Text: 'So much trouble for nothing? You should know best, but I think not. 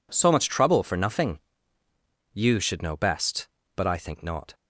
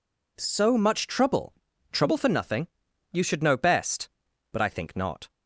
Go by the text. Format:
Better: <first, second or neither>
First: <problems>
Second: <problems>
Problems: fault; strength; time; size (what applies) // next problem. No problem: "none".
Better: first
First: none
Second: says "trouble" twice; at 1.9 s